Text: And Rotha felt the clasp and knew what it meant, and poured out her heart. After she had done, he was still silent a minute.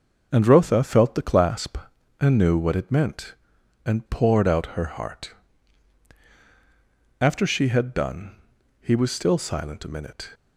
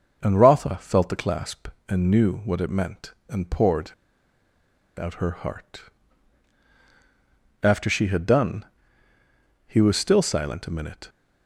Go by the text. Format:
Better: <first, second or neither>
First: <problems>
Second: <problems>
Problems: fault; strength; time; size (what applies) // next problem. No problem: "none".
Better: first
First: starts louder than the rest; until 1.3 s; 6 dB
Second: starts louder than the rest; noticeable; until 1.2 s; 6 dB // pauses between "poured" and "out"; at 3.9 s; 1.0 s long